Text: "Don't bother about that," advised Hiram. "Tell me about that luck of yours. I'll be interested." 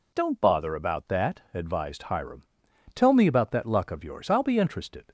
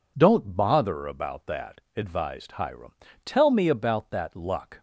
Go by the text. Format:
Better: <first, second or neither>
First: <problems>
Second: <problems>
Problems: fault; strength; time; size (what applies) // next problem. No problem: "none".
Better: first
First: none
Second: stops before "of yours I'll be interested"; at 4.7 s